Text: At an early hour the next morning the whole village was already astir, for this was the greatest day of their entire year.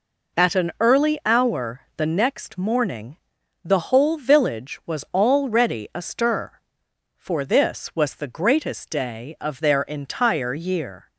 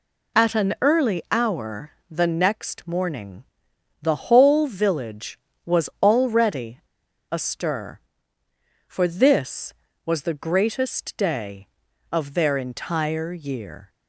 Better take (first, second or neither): first